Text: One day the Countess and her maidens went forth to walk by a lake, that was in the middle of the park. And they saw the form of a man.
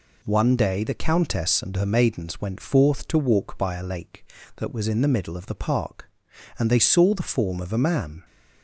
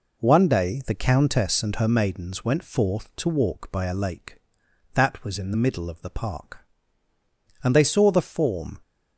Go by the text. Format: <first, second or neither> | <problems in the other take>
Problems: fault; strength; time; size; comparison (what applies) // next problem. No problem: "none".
first | stops before "of a man"; at 8.8 s